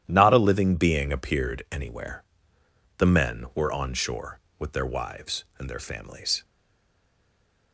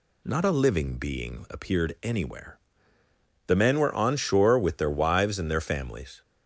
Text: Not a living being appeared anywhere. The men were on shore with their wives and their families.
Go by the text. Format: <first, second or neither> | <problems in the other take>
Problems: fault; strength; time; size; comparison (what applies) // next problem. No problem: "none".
second | starts louder than the rest; strong; until 1.0 s; 11 dB // stays silent after the last word; noticeable; from 6.4 s on; 1.3 s long